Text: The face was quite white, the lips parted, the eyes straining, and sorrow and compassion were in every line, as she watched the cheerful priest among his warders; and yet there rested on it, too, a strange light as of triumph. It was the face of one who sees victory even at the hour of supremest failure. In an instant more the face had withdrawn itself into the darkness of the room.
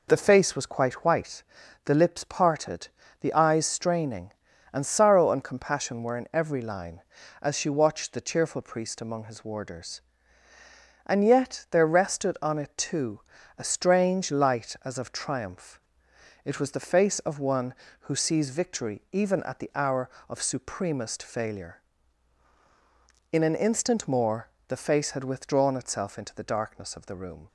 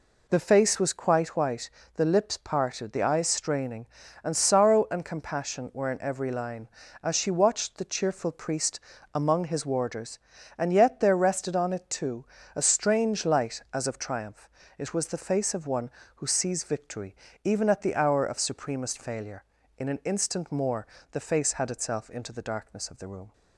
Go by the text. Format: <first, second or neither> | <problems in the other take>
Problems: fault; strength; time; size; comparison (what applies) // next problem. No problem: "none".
first | pauses between "priest" and "among"; slight; at 8.7 s; 0.34 s long // pauses between "victory" and "even"; slight; at 17.1 s; 0.30 s long // pauses between "more" and "the"; slight; at 20.8 s; 0.24 s long; slight in the first // skips "withdrawn"; at 21.7 s